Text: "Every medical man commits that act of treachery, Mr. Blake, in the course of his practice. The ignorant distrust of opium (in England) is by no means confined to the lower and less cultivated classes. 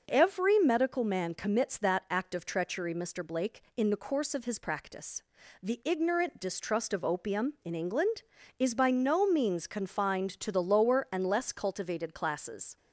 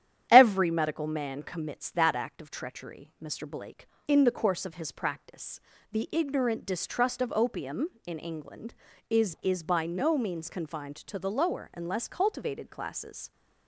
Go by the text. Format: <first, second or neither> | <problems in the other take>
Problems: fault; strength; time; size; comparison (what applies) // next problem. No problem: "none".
first | starts louder than the rest; strong; until 1.3 s; 10.5 dB; noticeable in the first // says "is" twice; at 9.4 s